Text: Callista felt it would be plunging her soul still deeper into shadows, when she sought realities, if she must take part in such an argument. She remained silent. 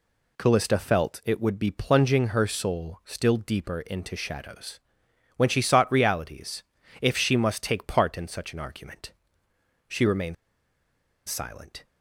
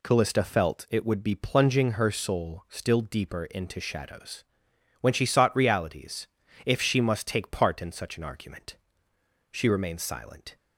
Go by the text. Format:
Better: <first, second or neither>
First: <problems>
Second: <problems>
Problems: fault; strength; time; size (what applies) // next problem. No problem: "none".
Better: second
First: pauses between "remained" and "silent"; noticeable; at 10.3 s; 0.93 s long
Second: none